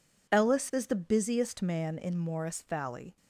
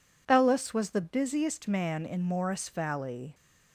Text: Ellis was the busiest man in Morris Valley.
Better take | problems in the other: second | says "is" for "was"; at 0.7 s

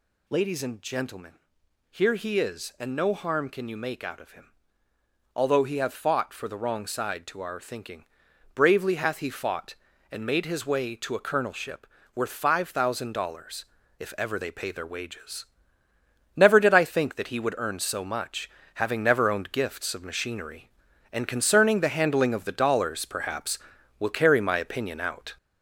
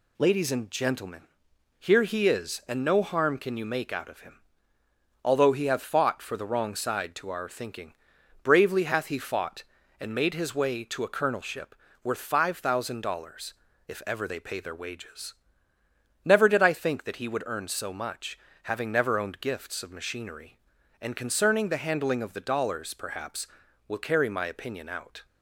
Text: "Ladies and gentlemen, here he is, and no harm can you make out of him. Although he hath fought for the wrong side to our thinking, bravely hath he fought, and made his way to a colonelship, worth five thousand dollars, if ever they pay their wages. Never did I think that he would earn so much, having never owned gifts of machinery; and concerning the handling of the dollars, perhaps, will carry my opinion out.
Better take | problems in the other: second | gets louder; noticeable; throughout; 5.5 dB

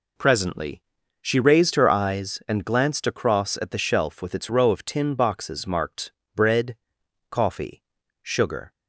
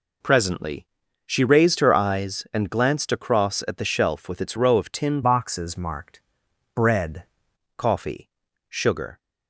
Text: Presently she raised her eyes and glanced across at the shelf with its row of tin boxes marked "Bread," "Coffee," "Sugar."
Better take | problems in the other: first | pauses between "Presently" and "she"; at 0.8 s; 0.40 s long; also in the first // changes voice from "boxes" to "Bread"; from 5.2 to 7.2 s; 2.0 s long // pauses between "marked" and "Bread"; noticeable; at 6.1 s; 0.56 s long; slight in the first

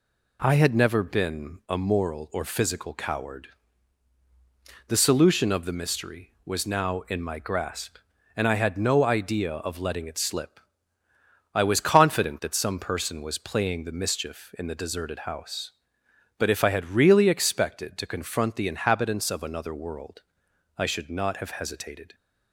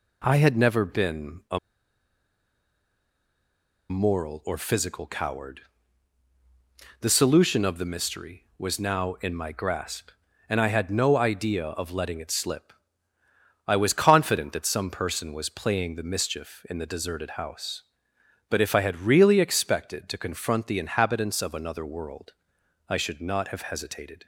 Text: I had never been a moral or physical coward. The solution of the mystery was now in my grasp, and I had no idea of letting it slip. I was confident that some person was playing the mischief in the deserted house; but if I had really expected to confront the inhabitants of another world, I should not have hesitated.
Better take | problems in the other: first | pauses between "a" and "moral"; strong; at 1.5 s; 2.3 s long

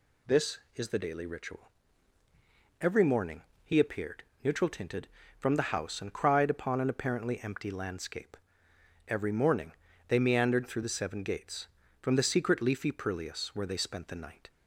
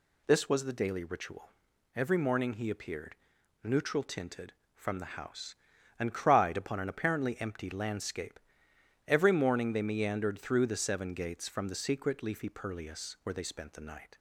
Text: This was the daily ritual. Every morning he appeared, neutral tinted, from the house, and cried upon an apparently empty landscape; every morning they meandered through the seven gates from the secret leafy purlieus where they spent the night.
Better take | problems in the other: second | says "is" for "was"; at 0.7 s // pauses between "morning" and "he"; slight; at 3.4 s; 0.20 s long // pauses between "morning" and "they"; slight; at 9.7 s; 0.34 s long

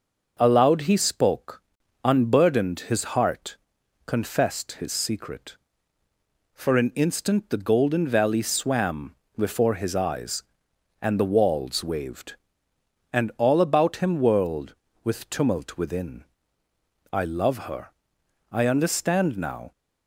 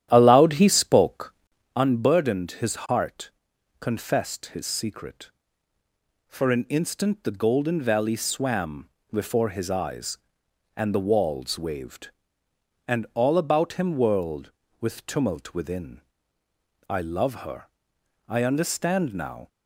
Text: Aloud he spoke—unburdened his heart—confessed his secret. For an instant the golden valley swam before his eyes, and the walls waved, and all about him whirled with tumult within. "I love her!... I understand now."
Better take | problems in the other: first | starts louder than the rest; strong; until 1.7 s; 11.5 dB // pauses between "swam" and "before"; slight; at 8.8 s; 0.24 s long; slight in the first

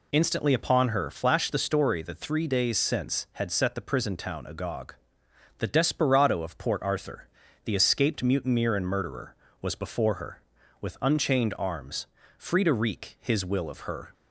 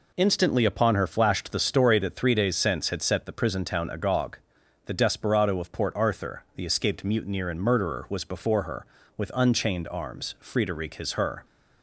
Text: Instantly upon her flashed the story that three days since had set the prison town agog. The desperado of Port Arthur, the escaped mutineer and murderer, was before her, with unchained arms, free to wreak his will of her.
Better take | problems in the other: first | skips "will of"; at 11.1 s

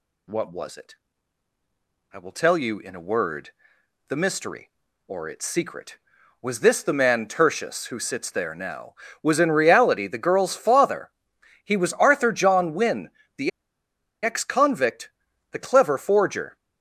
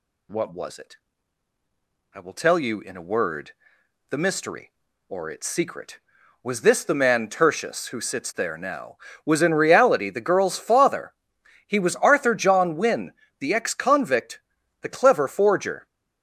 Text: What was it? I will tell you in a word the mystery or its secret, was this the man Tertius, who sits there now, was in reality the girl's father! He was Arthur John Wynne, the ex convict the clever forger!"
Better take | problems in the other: second | pauses between "word" and "the"; noticeable; at 3.4 s; 0.60 s long; noticeable in the second // pauses between "the" and "ex"; noticeable; at 13.5 s; 0.73 s long // pauses between "convict" and "the"; at 15.0 s; 0.40 s long; also in the second

